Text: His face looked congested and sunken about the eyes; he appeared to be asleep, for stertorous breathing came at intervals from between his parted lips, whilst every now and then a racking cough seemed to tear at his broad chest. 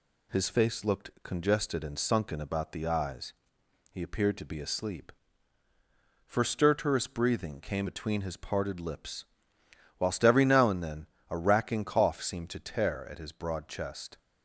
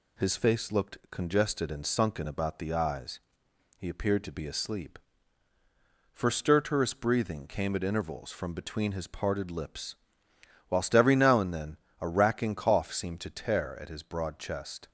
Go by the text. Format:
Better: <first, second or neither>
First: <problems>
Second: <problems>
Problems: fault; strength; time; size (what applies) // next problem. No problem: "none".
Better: second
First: skips "at intervals from"; at 7.8 s // pauses between "then" and "a"; slight; at 11.0 s; 0.24 s long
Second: pauses between "then" and "a"; slight; at 11.7 s; 0.24 s long